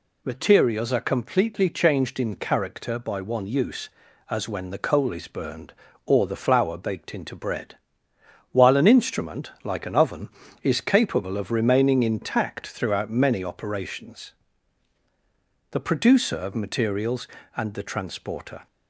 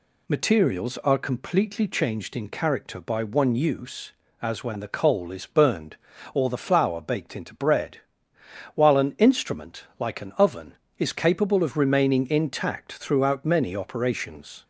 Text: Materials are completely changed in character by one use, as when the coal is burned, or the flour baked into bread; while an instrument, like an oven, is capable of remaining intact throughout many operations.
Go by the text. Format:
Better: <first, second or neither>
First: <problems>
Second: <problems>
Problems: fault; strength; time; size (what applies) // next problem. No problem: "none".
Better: second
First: goes on to say "The producer of materials and the transporter"; strong; from 15.7 s on; 2.9 s long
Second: none